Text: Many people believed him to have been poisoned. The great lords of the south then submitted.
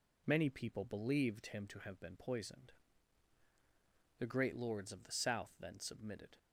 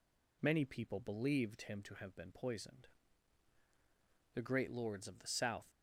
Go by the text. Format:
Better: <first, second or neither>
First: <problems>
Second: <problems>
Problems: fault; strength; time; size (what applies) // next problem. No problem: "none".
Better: first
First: none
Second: stops before "then submitted"; at 5.6 s